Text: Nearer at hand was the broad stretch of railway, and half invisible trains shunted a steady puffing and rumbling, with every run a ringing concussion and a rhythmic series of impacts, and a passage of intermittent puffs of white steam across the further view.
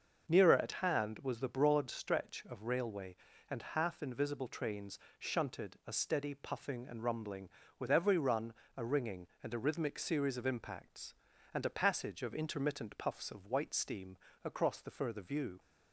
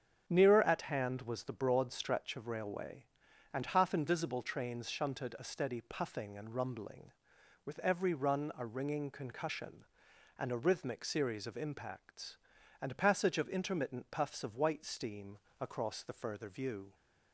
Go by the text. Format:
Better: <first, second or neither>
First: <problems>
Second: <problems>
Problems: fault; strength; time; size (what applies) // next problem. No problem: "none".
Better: second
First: starts louder than the rest; until 1.3 s; 6.5 dB // pauses between "trains" and "shunted"; slight; at 4.9 s; 0.22 s long // pauses between "run" and "a"; slight; at 8.5 s; 0.24 s long // skips "concussion"; at 9.3 s // pauses between "steam" and "across"; slight; at 14.1 s; 0.30 s long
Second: starts louder than the rest; strong; until 1.2 s; 7.5 dB // pauses between "steam" and "across"; slight; at 15.3 s; 0.24 s long